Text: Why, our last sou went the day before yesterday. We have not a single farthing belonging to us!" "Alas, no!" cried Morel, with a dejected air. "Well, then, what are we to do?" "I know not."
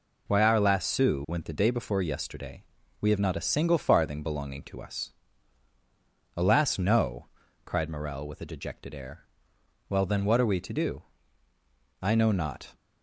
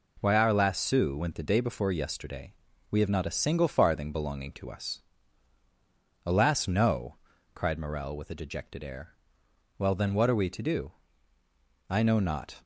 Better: second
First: loses the start of "Why"; at 0.2 s; 25 ms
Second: none

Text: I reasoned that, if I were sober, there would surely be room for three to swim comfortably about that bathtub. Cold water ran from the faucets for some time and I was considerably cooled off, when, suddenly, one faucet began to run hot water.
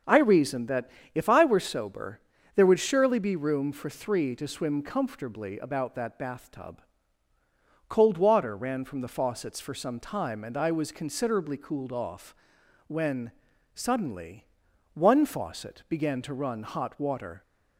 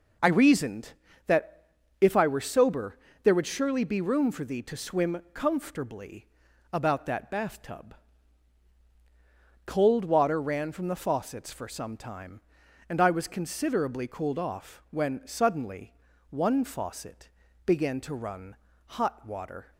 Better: first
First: none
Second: says "thee" for "three"; at 4.4 s // pauses between "comfortably" and "about"; noticeable; at 6.2 s; 0.46 s long // pauses between "faucet" and "began"; at 17.2 s; 0.38 s long // pauses between "run" and "hot"; slight; at 18.5 s; 0.30 s long

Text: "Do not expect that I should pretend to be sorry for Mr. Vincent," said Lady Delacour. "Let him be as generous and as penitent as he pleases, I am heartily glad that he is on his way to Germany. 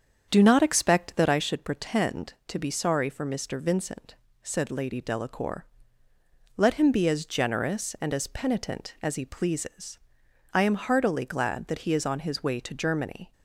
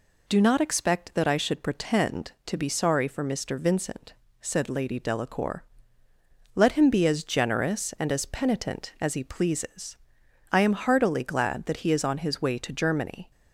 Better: second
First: starts louder than the rest; strong; until 1.5 s; 7.5 dB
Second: none

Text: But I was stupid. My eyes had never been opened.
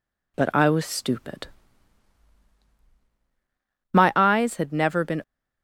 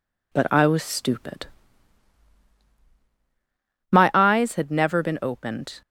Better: second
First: stops before "opened"; at 5.2 s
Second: none

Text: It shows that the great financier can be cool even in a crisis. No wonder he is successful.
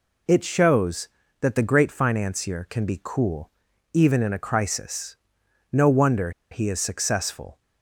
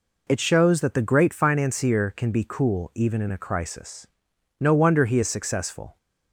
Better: second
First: pauses between "cool" and "even"; at 3.5 s; 0.44 s long // pauses between "wonder" and "he"; slight; at 6.3 s; 0.21 s long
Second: none

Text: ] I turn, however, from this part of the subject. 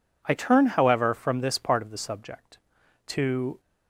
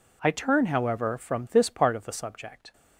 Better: second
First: goes on to say "To"; from 3.0 s on; 0.52 s long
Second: none

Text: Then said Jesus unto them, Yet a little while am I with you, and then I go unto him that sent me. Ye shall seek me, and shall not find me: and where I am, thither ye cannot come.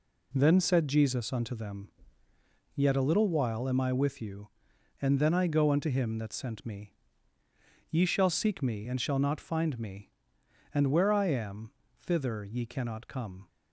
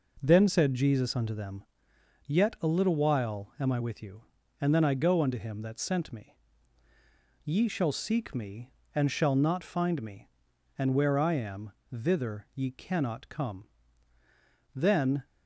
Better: first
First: none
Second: goes on to say "Then"; from 14.7 s on; 0.52 s long

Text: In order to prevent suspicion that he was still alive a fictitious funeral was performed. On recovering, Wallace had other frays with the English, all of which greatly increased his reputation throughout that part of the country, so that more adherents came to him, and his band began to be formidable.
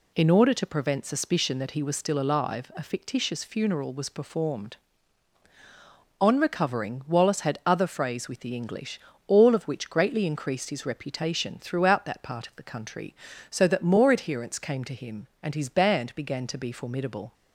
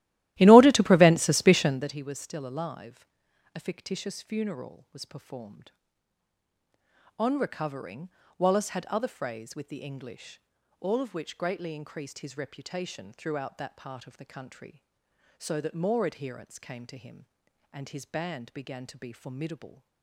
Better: first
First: none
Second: starts louder than the rest; strong; until 1.9 s; 15 dB // pauses between "alive" and "a"; noticeable; at 3.0 s; 0.48 s long

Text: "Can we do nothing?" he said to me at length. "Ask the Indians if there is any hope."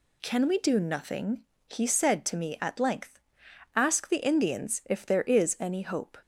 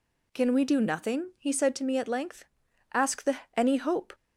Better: first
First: none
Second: skips "Indians if there is"; at 3.4 s

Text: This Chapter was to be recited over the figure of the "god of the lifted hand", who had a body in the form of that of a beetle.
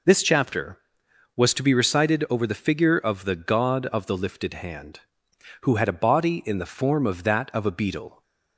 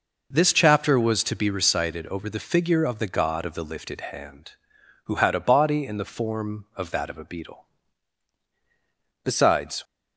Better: first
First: none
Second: goes on to say "Besides"; from 9.2 s on; 0.58 s long

